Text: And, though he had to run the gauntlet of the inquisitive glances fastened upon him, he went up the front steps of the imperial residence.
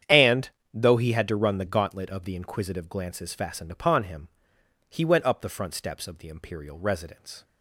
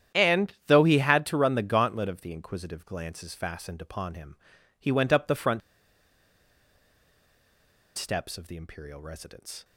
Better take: first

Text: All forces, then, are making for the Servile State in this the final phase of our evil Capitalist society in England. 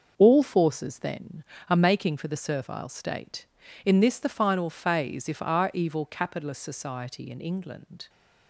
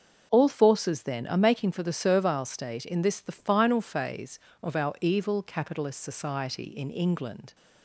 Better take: second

